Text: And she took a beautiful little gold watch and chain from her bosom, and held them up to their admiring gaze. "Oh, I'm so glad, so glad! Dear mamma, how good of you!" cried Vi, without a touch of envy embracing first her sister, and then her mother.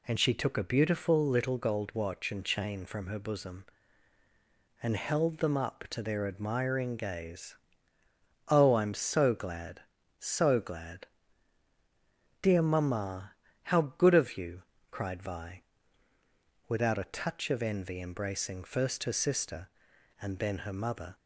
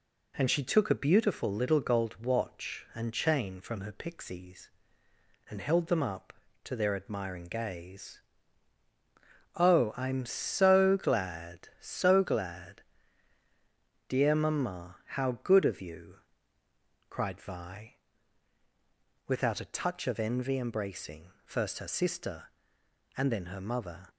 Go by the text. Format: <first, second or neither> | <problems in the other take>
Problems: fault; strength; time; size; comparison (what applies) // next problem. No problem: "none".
first | says "pixies" for "bosom"; at 3.9 s